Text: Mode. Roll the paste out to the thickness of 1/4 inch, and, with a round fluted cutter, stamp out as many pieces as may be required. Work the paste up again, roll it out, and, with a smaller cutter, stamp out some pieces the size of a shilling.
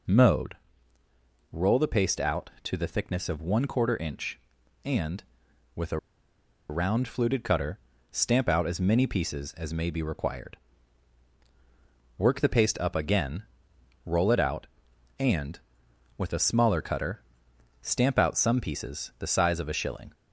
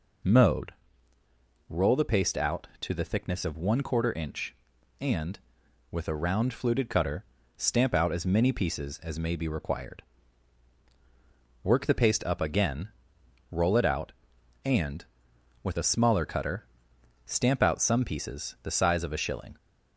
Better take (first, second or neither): second